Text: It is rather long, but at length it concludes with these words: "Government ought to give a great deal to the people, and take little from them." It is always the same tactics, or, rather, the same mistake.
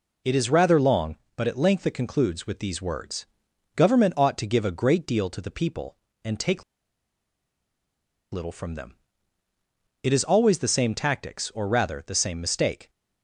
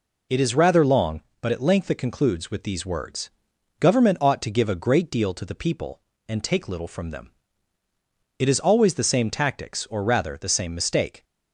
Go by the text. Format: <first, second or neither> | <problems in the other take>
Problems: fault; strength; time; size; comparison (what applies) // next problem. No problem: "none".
second | pauses between "take" and "little"; strong; at 6.6 s; 1.7 s long